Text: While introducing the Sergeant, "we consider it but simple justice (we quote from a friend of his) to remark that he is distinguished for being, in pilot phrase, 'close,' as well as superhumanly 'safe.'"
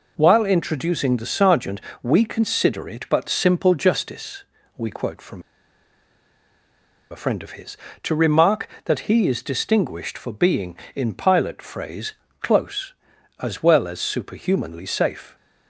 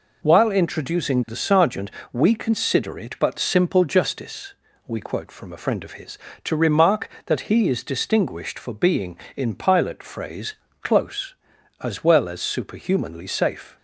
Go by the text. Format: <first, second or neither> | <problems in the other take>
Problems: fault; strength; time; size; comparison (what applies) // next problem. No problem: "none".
second | pauses between "from" and "a"; strong; at 5.4 s; 1.6 s long